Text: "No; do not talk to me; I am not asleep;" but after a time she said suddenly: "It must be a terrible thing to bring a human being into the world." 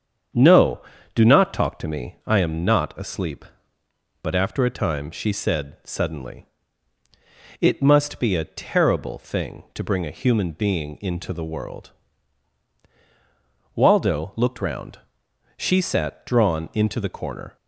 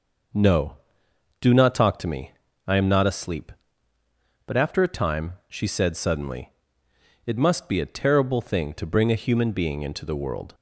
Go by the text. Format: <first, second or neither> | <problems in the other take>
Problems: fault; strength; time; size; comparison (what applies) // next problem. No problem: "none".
second | starts louder than the rest; strong; until 1.7 s; 7.5 dB // goes on to say "Waldo looked round she sat drawn into the corner"; strong; from 13.7 s on; 3.8 s long